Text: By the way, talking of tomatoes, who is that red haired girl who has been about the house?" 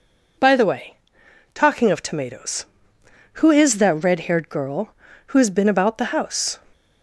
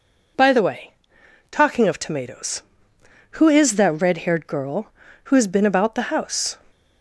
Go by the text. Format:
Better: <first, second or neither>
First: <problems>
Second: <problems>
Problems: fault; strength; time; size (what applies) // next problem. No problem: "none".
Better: neither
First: none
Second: none